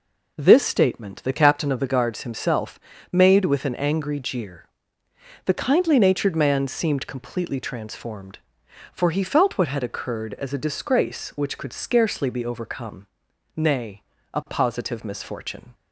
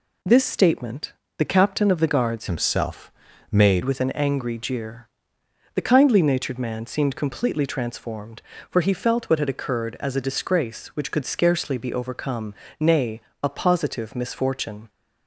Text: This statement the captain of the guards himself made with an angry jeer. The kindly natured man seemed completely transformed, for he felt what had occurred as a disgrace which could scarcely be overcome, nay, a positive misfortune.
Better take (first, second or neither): first